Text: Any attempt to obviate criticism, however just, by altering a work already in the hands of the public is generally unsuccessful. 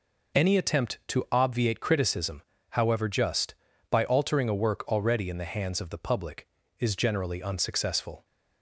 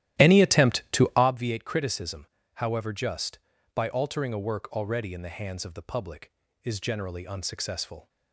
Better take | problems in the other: first | starts louder than the rest; strong; until 1.3 s; 13.5 dB

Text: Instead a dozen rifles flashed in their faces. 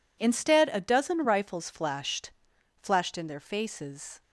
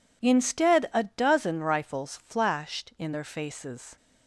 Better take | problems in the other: second | says "flashed" twice; at 2.7 s

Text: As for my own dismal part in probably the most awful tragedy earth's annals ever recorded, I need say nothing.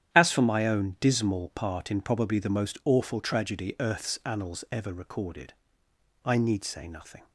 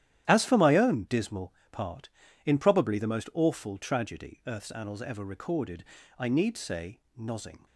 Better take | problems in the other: first | starts louder than the rest; strong; until 1.2 s; 11.5 dB; strong in the first // pauses between "dismal" and "part"; slight; at 1.5 s; 0.18 s long // says "nozzing" for "nothing"; at 7.1 s

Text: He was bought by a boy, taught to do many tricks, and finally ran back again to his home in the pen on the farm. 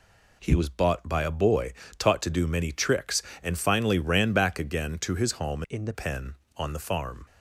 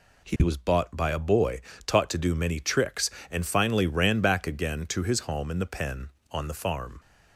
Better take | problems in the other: second | changes voice from "in" to "the"; from 5.6 to 5.9 s; 0.3 s long

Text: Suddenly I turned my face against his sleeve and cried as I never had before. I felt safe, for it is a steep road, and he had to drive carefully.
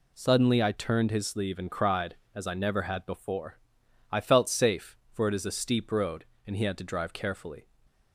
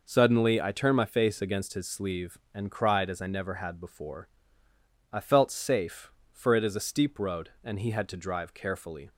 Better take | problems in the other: second | skips "my face against"; at 1.1 s // stays silent after the last word; slight; from 7.6 s on; 0.5 s long

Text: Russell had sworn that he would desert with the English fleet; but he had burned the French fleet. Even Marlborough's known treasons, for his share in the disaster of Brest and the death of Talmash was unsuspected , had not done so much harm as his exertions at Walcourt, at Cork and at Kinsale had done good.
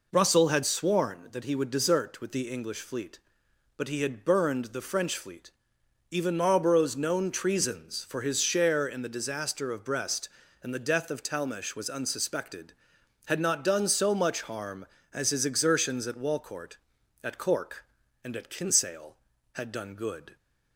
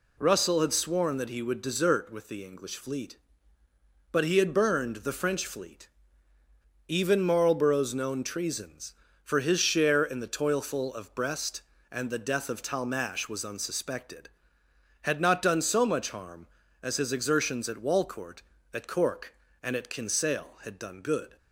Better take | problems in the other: first | says "toilful" for "disaster"; at 10.2 s

